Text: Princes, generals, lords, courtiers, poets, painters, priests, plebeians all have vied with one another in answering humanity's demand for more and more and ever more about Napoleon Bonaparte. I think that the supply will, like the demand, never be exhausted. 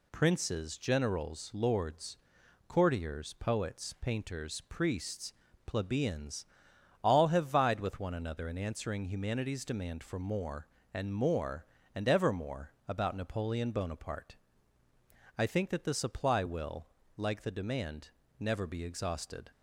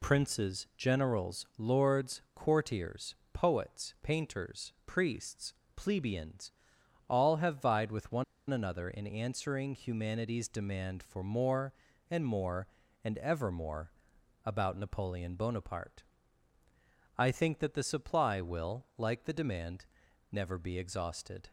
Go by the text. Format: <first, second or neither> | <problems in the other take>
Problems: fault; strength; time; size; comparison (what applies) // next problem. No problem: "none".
first | pauses between "plebeians" and "all"; noticeable; at 6.5 s; 0.58 s long; noticeable in the first // pauses between "one" and "another"; slight; at 8.2 s; 0.26 s long // pauses between "more" and "about"; noticeable; at 13.9 s; 0.52 s long; slight in the first